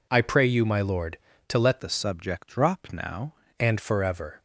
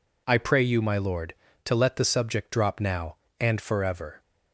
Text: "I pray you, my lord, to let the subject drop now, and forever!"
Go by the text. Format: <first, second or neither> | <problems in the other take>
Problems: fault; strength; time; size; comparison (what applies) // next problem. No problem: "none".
second | changes voice from "the" to "now"; from 1.8 to 3.3 s; 1.5 s long